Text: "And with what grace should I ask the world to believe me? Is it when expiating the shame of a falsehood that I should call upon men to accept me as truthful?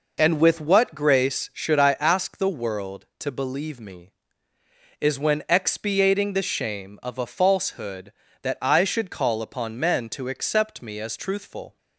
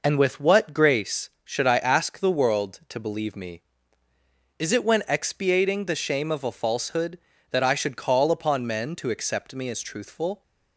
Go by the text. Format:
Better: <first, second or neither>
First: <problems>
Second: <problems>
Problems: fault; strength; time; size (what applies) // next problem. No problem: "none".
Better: second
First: skips "it"; at 5.1 s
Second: none